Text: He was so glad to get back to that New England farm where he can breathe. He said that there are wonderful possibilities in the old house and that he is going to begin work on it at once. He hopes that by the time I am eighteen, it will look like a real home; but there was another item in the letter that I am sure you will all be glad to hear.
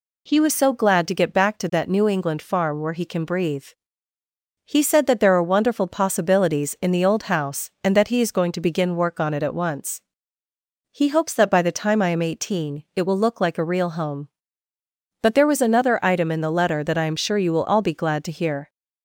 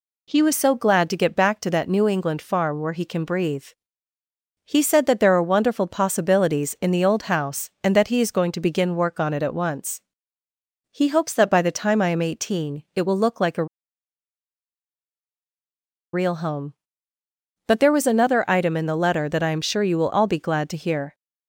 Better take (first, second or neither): first